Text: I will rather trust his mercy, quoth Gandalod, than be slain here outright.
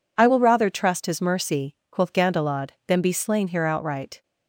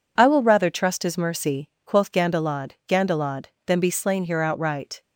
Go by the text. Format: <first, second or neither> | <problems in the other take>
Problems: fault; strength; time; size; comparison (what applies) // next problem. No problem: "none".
first | says "Gandalod" twice; at 2.8 s